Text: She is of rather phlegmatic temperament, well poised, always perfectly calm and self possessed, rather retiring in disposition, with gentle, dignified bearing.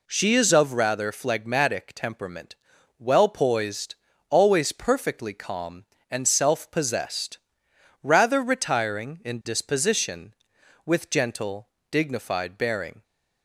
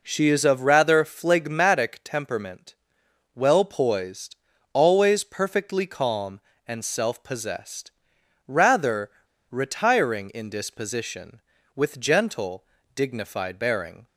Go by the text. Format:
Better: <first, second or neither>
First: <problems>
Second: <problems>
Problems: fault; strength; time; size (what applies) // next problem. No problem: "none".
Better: first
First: none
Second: pauses between "rather" and "retiring"; at 9.0 s; 0.41 s long